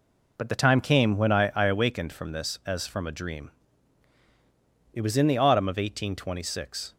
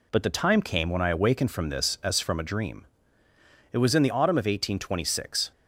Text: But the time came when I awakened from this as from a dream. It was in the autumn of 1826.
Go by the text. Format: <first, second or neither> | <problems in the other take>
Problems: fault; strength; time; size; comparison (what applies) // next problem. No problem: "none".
second | says "I" twice; at 1.5 s